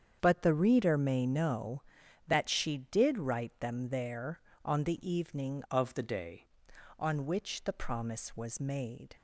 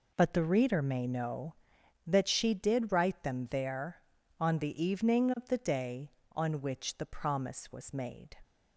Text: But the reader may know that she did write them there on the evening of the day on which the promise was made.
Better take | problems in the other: second | starts louder than the rest; strong; until 1.2 s; 7.5 dB // changes voice from "of" to "day"; from 5.6 to 6.4 s; 0.8 s long

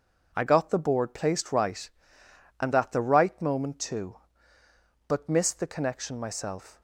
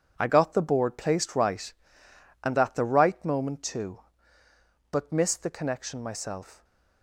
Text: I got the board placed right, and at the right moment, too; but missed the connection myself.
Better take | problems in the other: first | gets quieter; strong; throughout; 10.5 dB

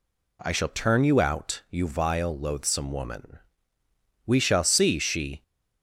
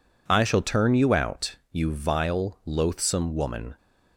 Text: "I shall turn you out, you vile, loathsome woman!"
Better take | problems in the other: second | goes on to say "We shall see she"; noticeable; from 4.2 s on; 1.1 s long

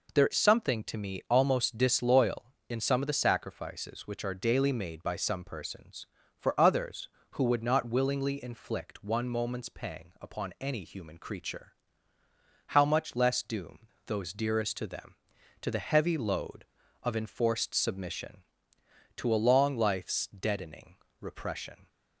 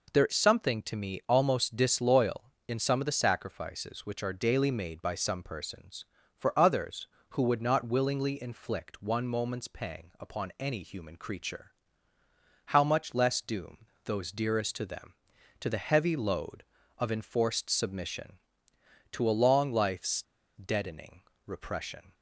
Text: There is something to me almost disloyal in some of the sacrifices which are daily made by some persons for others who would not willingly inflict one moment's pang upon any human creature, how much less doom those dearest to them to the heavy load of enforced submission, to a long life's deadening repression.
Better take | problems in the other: first | pauses between "doom" and "those"; slight; at 13.8 s; 0.20 s long; slight in the first // pauses between "life's" and "deadening"; slight; at 20.2 s; 0.32 s long // pauses between "deadening" and "repression"; slight; at 21.2 s; 0.24 s long; slight in the first

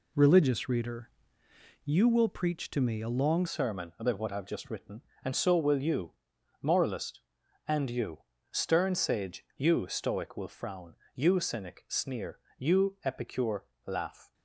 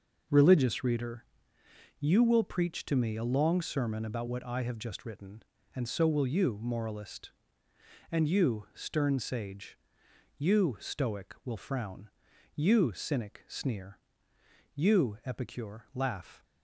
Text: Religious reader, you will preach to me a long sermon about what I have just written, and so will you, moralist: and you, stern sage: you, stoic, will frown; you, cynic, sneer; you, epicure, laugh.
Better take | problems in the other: second | changes voice at "sermon"; from 3.4 s on; 10.9 s long

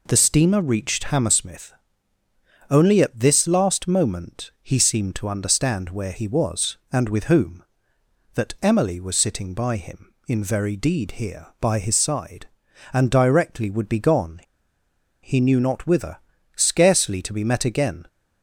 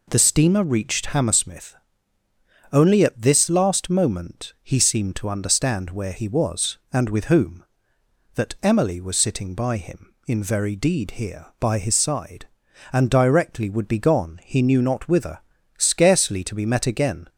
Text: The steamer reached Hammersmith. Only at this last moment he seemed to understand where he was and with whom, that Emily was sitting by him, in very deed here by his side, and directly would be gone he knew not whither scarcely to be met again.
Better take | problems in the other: second | pauses between "gone" and "he"; noticeable; at 14.4 s; 0.82 s long // pauses between "whither" and "scarcely"; at 16.1 s; 0.38 s long; also in the second

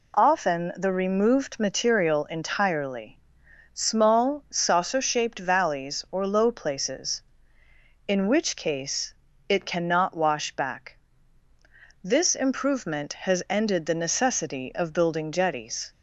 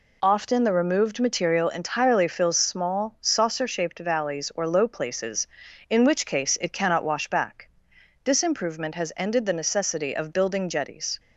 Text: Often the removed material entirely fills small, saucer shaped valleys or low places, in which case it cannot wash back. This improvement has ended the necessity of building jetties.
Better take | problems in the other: second | skips "fills"; at 3.4 s // pauses between "case" and "it"; slight; at 9.1 s; 0.36 s long

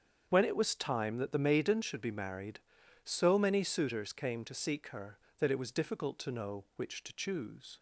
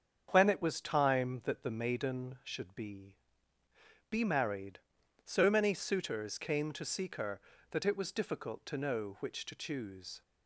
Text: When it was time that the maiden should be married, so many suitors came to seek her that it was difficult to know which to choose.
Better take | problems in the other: first | starts louder than the rest; strong; until 1.3 s; 7.5 dB; strong in the first // says "be" twice; at 4.1 s

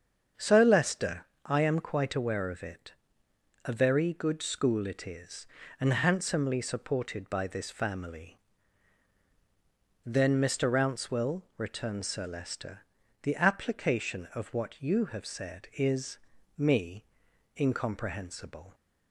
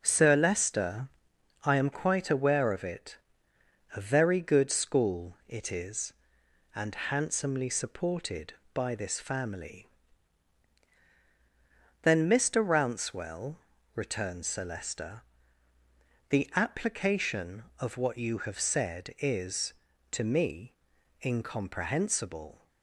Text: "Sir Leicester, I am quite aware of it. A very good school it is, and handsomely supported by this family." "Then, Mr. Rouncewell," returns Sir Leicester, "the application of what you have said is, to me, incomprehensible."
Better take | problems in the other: second | starts louder than the rest; until 1.5 s; 7 dB; noticeable in the second // skips "to"; at 16.3 s

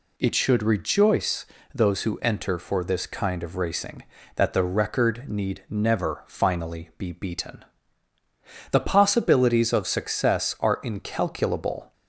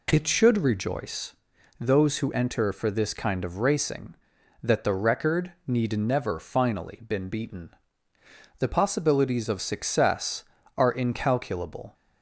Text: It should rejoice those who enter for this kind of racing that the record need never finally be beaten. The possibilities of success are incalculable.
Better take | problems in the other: first | pauses between "rejoice" and "those"; at 1.3 s; 0.44 s long; slight in the first // pauses between "record" and "need"; slight; at 5.5 s; 0.16 s long // says "been" for "be"; at 7.0 s

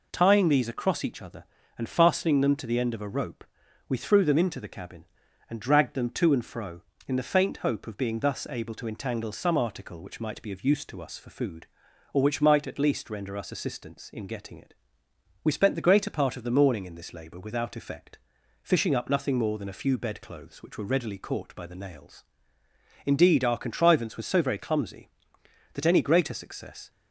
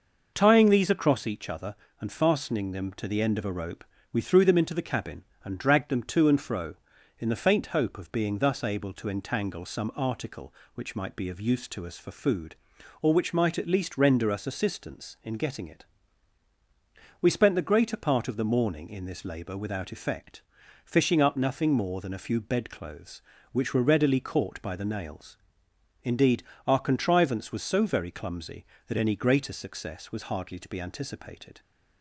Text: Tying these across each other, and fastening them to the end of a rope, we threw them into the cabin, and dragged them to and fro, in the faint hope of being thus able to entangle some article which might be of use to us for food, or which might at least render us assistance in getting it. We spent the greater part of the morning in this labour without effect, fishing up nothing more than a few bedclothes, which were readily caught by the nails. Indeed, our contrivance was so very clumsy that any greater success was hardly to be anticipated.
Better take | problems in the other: second | stops before "was hardly to be anticipated"; at 26.8 s

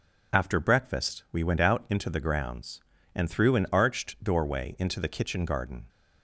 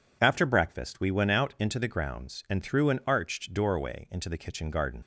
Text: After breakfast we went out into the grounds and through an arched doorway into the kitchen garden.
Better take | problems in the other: first | leaves "garden" unfinished; at 5.0 s; 45 ms

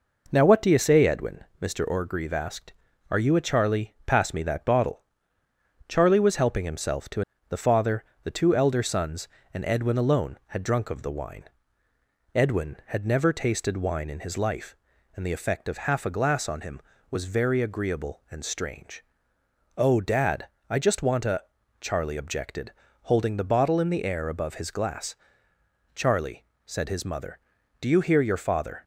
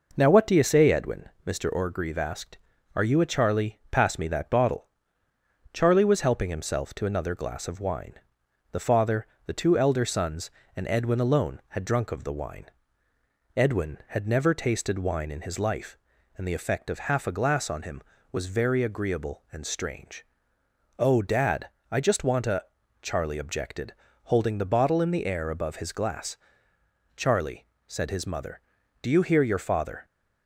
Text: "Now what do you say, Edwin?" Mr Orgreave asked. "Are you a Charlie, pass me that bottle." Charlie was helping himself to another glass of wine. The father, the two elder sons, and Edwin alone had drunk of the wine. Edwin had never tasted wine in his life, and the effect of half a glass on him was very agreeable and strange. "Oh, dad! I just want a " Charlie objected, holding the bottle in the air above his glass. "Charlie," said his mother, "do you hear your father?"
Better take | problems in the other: second | skips "another glass of wine"; at 7.3 s

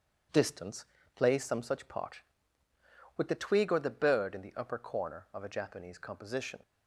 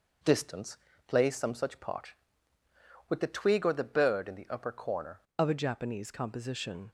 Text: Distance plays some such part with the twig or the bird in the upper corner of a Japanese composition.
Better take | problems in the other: first | pauses between "Distance" and "plays"; slight; at 0.7 s; 0.30 s long; slight in the first // changes voice at "of"; from 5.3 s on; 1.6 s long

